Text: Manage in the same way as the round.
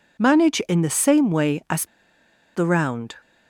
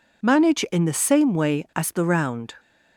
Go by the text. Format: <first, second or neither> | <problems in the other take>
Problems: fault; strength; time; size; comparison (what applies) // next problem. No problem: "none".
second | pauses between "as" and "the"; noticeable; at 1.8 s; 0.69 s long